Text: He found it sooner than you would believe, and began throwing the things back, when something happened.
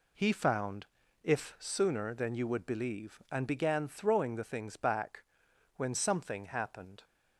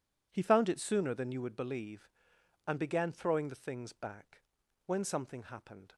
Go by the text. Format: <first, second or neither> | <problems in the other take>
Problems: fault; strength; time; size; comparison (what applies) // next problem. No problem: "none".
second | says "if" for "it"; at 1.2 s